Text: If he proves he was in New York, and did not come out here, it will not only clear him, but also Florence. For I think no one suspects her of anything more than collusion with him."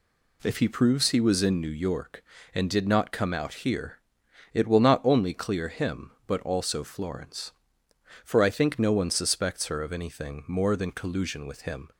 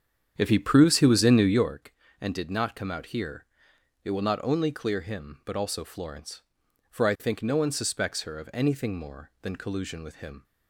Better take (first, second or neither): first